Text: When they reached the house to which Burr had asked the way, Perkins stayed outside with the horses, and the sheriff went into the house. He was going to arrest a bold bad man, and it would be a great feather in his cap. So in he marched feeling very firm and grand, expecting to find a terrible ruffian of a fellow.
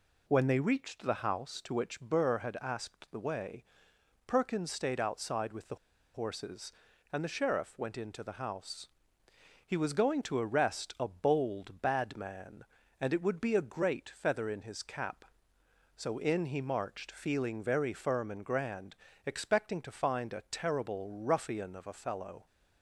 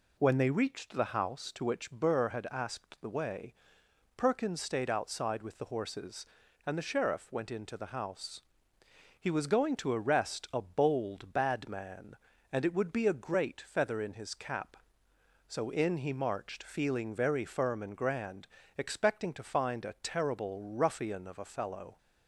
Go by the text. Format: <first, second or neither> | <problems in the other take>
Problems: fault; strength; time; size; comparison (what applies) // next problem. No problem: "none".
second | pauses between "the" and "horses"; at 5.7 s; 0.38 s long